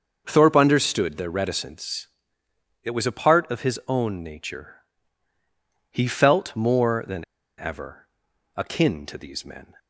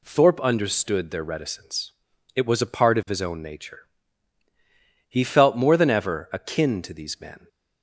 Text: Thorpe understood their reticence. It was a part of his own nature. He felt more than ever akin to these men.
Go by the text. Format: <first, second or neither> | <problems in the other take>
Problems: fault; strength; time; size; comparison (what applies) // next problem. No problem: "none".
second | starts louder than the rest; until 1.2 s; 6.5 dB // pauses between "than" and "ever"; slight; at 7.2 s; 0.33 s long // pauses between "ever" and "akin"; noticeable; at 8.0 s; 0.48 s long